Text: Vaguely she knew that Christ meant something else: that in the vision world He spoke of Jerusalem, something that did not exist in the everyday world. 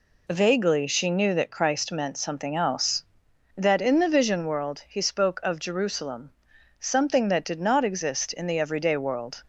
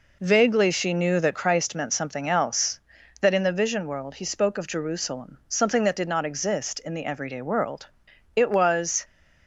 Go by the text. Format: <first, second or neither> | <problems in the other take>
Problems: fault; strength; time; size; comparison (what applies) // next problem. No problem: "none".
first | goes on to say "It was"; noticeable; from 8.3 s on; 0.70 s long